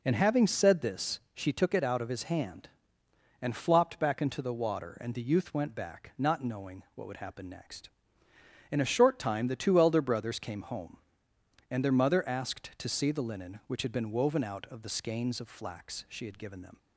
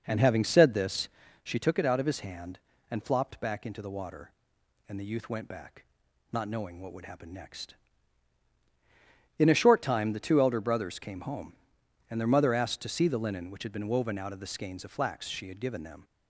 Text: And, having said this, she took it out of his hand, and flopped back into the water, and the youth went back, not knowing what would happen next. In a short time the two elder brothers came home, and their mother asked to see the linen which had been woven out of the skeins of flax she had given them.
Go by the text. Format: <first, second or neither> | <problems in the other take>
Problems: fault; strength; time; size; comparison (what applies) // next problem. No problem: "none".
first | starts louder than the rest; noticeable; until 1.4 s; 5.5 dB